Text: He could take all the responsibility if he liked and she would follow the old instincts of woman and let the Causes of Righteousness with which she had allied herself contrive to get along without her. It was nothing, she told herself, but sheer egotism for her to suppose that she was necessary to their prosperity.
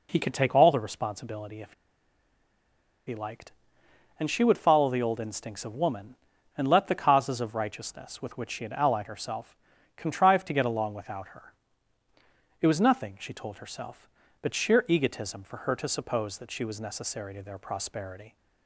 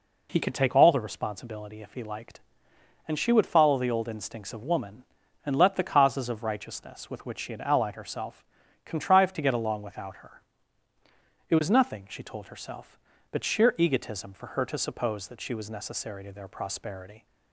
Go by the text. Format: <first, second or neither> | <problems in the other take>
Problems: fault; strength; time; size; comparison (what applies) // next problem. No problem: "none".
second | pauses between "if" and "he"; strong; at 1.7 s; 1.3 s long // pauses between "herself" and "contrive"; at 9.5 s; 0.40 s long; also in the second